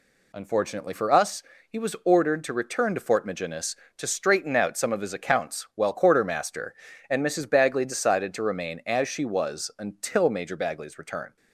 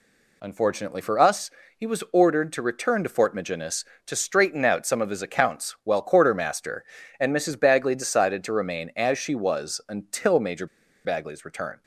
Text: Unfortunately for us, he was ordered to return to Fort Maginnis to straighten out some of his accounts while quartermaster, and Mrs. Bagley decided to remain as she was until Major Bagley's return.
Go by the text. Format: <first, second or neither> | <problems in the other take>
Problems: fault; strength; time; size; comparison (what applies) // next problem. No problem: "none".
first | pauses between "Major" and "Bagley's"; at 10.6 s; 0.38 s long